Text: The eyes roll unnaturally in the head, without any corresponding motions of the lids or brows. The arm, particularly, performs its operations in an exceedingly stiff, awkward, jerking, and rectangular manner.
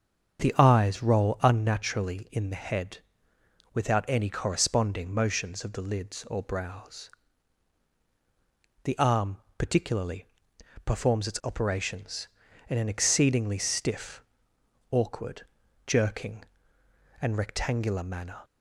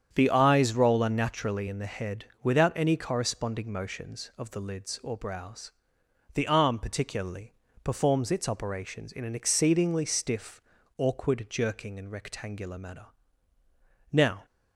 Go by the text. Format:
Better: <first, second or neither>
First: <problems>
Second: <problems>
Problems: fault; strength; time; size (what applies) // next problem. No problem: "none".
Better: first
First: starts louder than the rest; strong; until 1.4 s; 7.5 dB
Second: starts louder than the rest; strong; until 1.1 s; 8.5 dB // goes on to say "Now"; slight; from 14.1 s on; 0.34 s long